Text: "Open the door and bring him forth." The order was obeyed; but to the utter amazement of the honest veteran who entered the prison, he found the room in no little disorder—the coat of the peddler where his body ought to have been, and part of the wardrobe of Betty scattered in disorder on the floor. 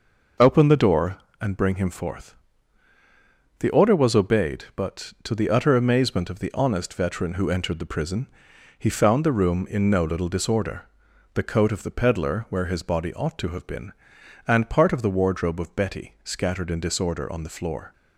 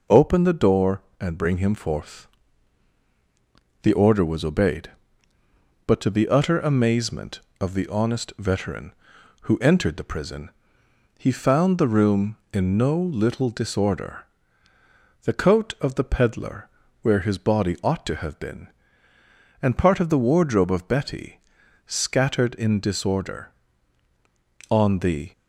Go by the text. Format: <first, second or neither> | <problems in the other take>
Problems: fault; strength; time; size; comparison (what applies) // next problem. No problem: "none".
first | pauses between "peddler" and "where"; slight; at 16.6 s; 0.32 s long // pauses between "Betty" and "scattered"; noticeable; at 21.3 s; 0.46 s long // stops before "floor"; at 25.3 s